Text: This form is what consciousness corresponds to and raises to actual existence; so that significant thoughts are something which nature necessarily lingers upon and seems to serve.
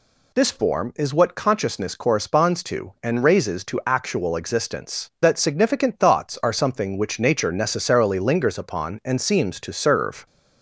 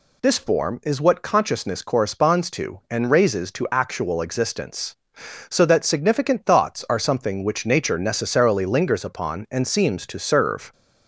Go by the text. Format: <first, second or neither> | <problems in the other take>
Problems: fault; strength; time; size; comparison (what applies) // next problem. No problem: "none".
second | skips "so"; at 5.1 s